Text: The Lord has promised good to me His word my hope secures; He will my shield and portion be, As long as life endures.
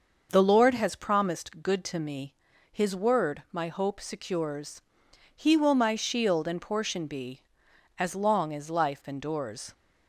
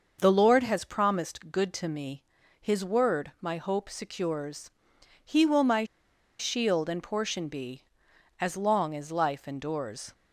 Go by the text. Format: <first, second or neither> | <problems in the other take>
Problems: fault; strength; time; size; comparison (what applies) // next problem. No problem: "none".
first | starts louder than the rest; until 1.2 s; 6 dB; also in the first // pauses between "me" and "His"; slight; at 2.2 s; 0.36 s long; slight in the first // pauses between "my" and "shield"; noticeable; at 5.8 s; 0.53 s long